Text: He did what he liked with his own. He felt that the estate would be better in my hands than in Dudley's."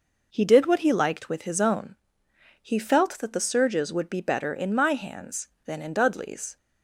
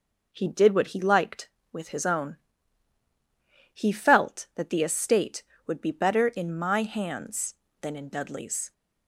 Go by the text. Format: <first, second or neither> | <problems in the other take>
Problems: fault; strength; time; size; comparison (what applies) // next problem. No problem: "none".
second | says "surges" for "estate"; at 3.4 s